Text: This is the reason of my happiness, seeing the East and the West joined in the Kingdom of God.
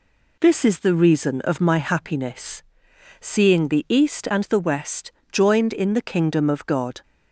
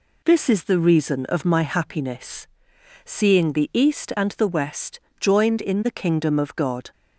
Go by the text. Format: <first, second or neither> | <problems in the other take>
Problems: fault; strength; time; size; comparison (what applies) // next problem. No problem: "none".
neither | pauses between "West" and "joined"; slight; the same in both